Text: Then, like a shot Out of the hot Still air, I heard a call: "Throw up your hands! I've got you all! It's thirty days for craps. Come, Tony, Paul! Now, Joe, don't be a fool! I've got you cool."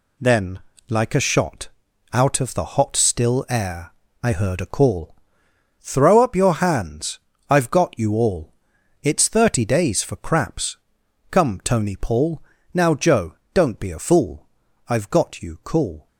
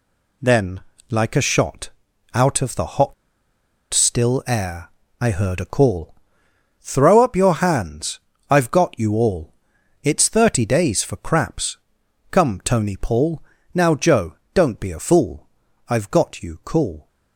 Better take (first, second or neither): first